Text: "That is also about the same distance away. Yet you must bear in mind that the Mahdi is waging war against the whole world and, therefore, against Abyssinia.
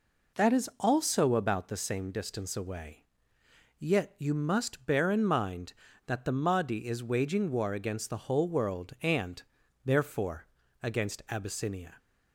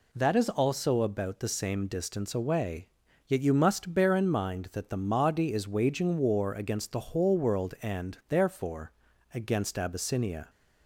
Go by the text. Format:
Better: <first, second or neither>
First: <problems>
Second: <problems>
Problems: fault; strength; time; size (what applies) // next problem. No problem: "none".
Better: neither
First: none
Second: none